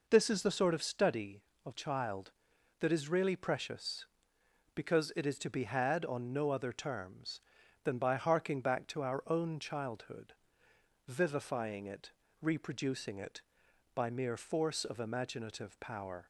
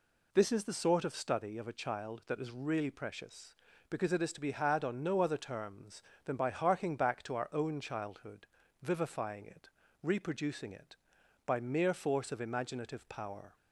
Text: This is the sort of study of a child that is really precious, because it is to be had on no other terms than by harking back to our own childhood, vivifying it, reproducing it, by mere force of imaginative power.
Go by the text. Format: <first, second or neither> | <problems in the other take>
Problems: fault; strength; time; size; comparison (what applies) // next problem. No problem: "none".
second | skips "a"; at 1.7 s